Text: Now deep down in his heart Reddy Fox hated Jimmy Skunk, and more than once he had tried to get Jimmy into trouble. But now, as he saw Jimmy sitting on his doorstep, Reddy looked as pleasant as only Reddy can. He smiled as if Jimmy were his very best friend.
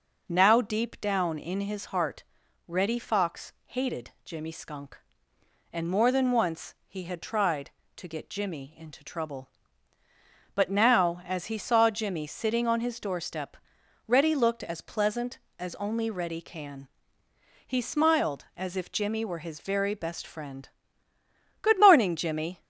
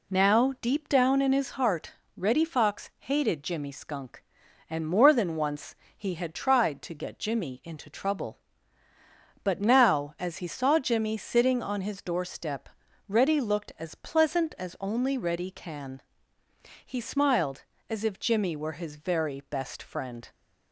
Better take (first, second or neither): second